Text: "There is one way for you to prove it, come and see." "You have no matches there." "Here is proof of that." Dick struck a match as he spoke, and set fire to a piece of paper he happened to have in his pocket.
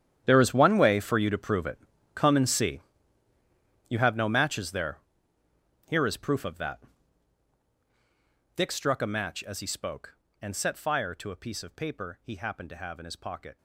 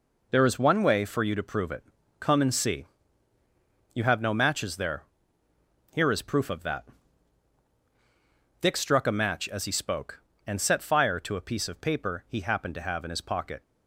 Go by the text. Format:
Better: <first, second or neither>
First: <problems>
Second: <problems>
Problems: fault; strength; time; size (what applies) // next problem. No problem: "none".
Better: second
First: gets quieter; strong; throughout; 17.5 dB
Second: none